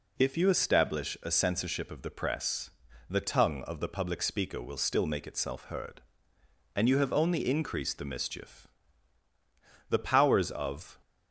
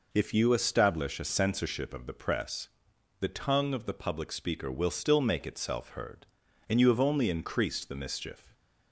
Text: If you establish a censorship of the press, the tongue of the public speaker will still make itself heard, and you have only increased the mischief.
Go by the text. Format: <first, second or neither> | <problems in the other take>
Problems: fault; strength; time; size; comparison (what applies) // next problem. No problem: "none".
second | goes on to say "The powers of"; noticeable; from 9.9 s on; 1.0 s long